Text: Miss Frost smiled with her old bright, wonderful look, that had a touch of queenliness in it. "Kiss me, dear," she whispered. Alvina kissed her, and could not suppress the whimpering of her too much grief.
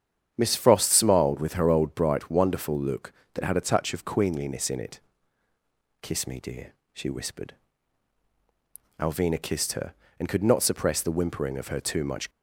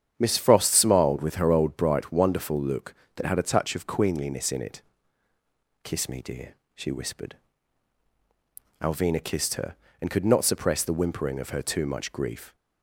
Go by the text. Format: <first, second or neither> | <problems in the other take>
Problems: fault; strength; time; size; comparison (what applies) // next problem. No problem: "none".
second | starts louder than the rest; strong; until 1.3 s; 8.5 dB; strong in the second // stops before "grief"; at 12.3 s